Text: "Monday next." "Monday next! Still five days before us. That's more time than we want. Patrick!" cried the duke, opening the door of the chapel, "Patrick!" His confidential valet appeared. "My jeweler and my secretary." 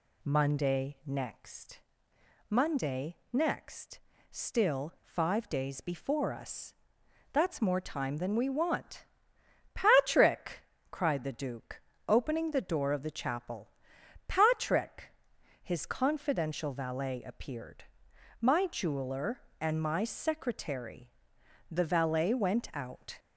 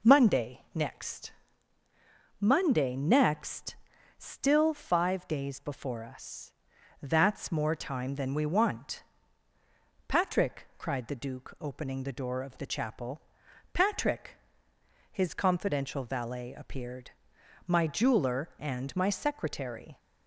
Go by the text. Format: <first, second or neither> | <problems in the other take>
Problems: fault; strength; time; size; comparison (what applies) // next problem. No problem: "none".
second | pauses between "Monday" and "next"; slight; at 3.1 s; 0.16 s long // goes on to say "The valet went out"; from 21.6 s on; 1.5 s long